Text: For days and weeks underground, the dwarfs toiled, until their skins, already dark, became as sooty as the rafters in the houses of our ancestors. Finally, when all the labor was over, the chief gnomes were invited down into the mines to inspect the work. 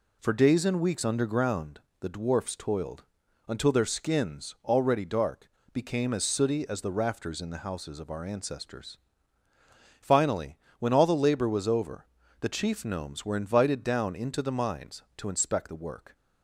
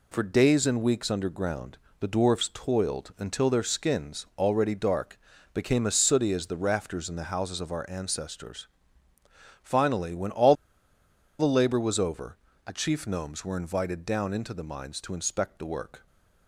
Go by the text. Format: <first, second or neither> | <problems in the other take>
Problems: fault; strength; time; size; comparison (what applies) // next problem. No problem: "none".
first | pauses between "all" and "the"; noticeable; at 10.5 s; 0.84 s long